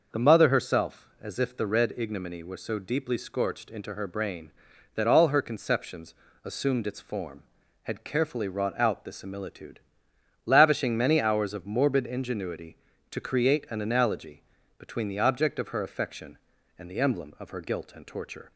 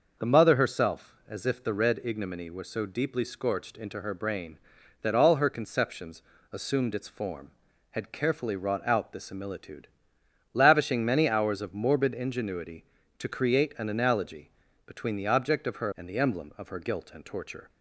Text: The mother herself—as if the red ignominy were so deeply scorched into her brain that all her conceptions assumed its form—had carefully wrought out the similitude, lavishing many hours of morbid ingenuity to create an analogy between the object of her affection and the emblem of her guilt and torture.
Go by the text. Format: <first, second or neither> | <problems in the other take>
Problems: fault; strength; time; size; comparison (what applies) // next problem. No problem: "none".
first | starts louder than the rest; noticeable; until 1.3 s; 6 dB; noticeable in the first // pauses between "conceptions" and "assumed"; slight; at 6.2 s; 0.28 s long; slight in the first // pauses between "analogy" and "between"; slight; at 14.5 s; 0.36 s long; slight in the first // skips "affection"; at 15.9 s